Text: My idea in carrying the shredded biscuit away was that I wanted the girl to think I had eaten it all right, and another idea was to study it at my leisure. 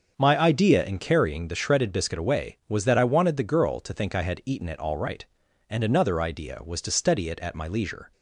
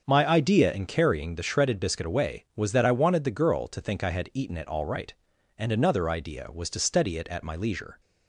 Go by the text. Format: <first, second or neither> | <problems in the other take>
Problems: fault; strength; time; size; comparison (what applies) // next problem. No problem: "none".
neither | starts louder than the rest; the same in both